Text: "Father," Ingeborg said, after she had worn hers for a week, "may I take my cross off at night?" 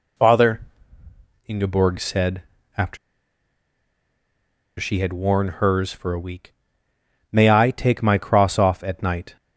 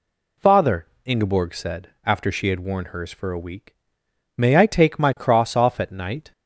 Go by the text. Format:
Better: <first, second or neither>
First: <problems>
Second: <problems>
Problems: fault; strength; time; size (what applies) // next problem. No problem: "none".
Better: second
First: pauses between "after" and "she"; strong; at 2.9 s; 1.8 s long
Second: none